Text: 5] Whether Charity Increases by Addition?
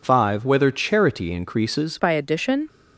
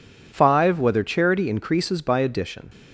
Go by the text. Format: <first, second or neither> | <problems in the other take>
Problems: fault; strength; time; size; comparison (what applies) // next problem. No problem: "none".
second | changes voice at "by"; from 1.9 s on; 0.7 s long